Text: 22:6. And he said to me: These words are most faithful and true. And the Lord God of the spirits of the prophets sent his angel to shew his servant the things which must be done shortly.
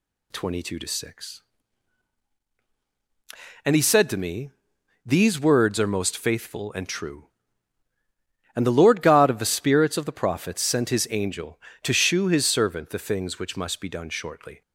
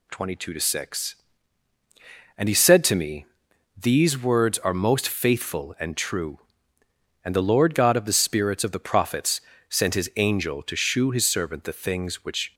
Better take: first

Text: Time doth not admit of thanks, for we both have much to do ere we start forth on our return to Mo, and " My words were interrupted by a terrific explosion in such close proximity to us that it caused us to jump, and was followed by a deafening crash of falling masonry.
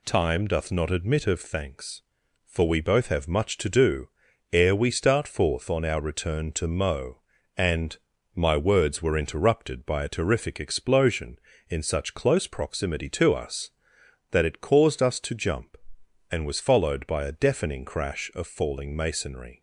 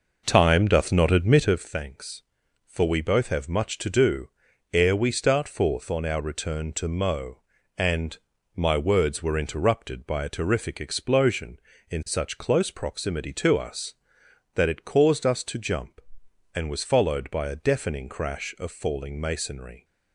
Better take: first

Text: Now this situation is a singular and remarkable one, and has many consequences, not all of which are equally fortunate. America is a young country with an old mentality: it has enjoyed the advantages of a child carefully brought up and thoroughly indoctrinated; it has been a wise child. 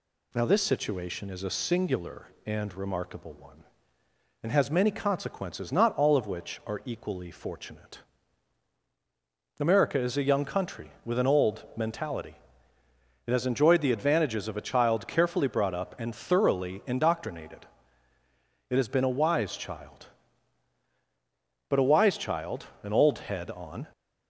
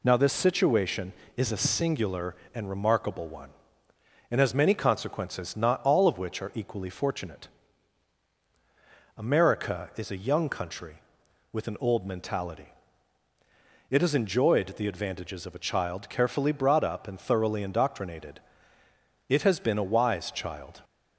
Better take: second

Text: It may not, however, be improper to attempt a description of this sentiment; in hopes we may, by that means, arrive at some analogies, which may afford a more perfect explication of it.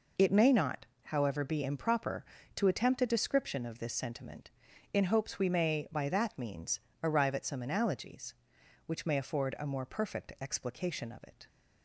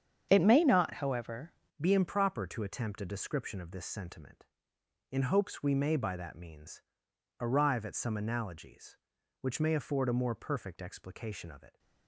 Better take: first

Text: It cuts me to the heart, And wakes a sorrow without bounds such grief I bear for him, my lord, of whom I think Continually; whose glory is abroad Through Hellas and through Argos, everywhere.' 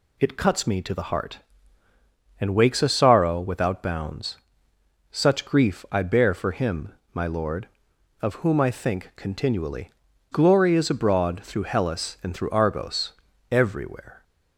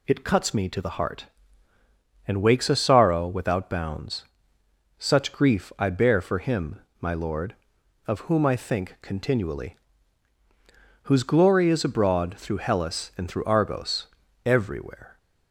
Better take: second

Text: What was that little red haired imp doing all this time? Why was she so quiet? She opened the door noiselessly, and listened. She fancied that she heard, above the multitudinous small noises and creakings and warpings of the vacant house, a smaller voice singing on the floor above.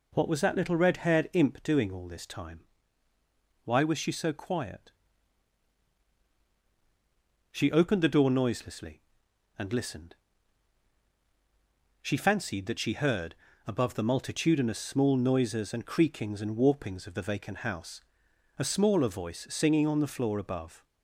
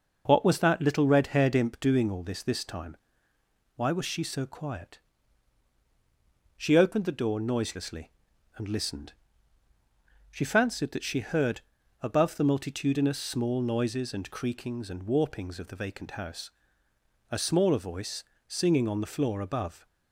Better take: first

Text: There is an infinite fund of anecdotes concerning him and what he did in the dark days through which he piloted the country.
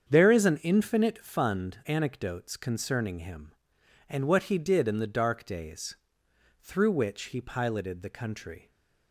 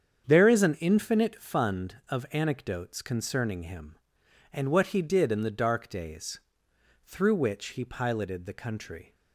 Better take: second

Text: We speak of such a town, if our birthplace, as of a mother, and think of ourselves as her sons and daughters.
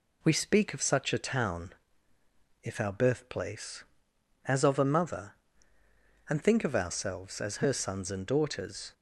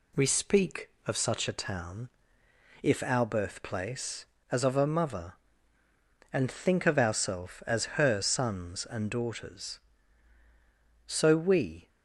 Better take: first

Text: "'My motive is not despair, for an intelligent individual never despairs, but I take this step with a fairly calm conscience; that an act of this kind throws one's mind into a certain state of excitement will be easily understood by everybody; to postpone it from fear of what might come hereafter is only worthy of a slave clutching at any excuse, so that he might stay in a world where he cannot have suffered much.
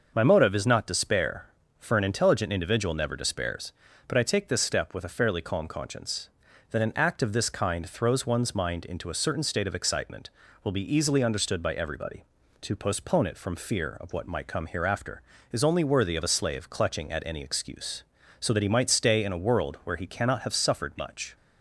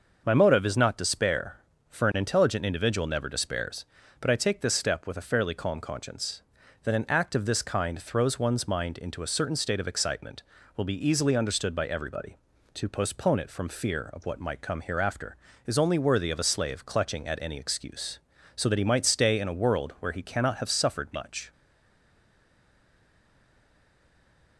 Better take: first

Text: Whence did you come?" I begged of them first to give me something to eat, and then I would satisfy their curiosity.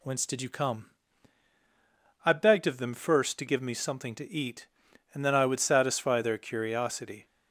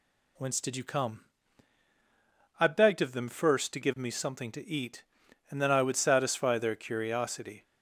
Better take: neither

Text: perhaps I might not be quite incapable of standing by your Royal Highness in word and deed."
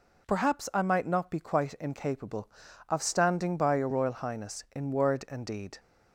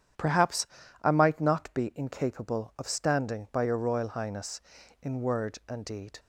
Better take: first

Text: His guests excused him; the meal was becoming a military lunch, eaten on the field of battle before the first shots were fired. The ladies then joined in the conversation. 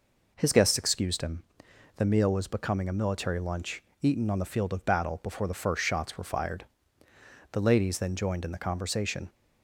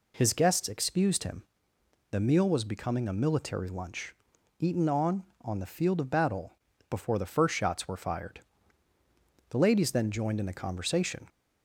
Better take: first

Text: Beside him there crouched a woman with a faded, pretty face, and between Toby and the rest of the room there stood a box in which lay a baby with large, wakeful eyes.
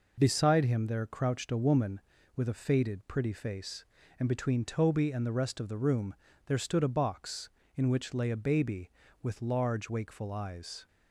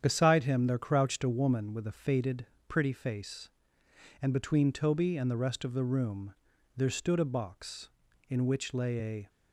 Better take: first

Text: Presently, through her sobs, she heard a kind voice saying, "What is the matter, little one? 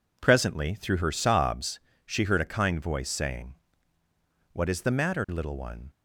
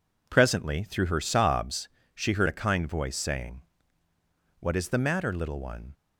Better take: neither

